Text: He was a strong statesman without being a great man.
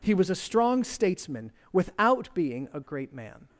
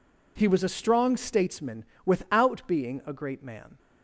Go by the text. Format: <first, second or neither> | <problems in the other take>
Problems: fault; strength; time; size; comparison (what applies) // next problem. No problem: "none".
neither | pauses between "statesman" and "without"; slight; the same in both